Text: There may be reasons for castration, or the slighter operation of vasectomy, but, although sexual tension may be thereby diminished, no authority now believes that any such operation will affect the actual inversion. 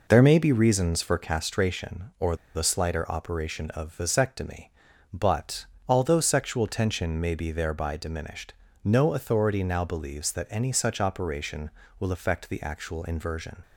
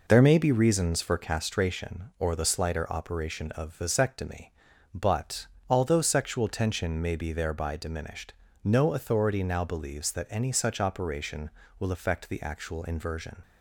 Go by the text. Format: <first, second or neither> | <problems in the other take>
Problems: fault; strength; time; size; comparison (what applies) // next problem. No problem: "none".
second | pauses between "or" and "the"; slight; at 2.3 s; 0.20 s long